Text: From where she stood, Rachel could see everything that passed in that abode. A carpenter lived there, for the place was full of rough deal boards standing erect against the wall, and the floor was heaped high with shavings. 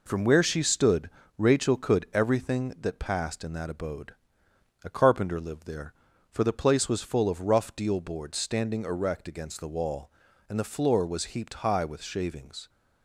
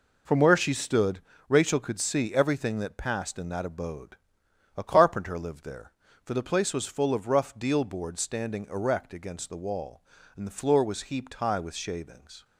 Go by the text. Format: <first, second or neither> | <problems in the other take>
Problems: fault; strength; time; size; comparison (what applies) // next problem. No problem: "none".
second | skips "see"; at 2.0 s